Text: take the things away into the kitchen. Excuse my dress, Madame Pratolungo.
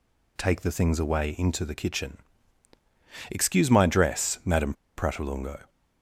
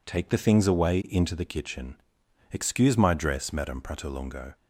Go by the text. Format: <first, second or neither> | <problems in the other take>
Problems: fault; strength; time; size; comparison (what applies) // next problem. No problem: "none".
second | pauses between "Madame" and "Pratolungo"; slight; at 4.7 s; 0.24 s long